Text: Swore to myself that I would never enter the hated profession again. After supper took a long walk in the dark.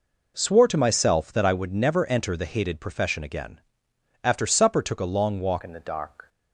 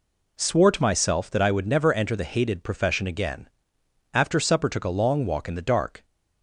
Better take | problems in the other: second | changes voice at "in"; from 5.6 s on; 0.6 s long

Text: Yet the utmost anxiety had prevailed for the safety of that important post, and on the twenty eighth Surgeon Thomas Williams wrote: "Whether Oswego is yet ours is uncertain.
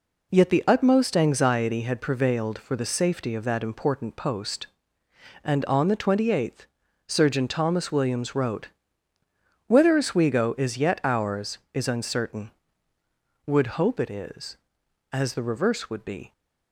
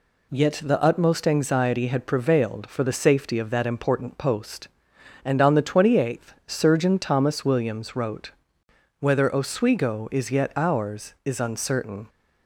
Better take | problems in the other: second | pauses between "eighth" and "Surgeon"; at 6.6 s; 0.42 s long // goes on to say "Would hope it is as the reverse would be"; strong; from 13.4 s on; 2.8 s long

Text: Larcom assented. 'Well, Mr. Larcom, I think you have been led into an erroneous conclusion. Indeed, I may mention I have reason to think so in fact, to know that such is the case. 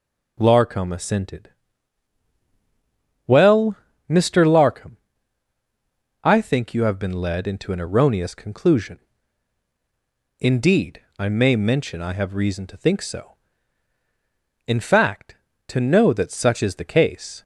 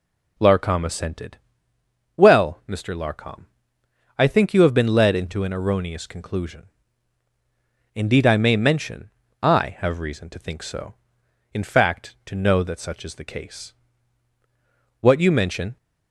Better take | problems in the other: first | pauses between "mention" and "I"; slight; at 9.1 s; 0.32 s long // goes on to say "What you mention"; noticeable; from 15.0 s on; 0.76 s long

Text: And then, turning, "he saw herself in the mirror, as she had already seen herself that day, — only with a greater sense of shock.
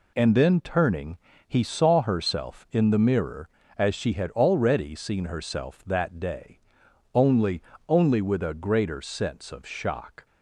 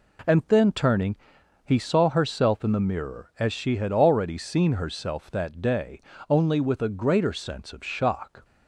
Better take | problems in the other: second | says "only" twice; at 7.8 s

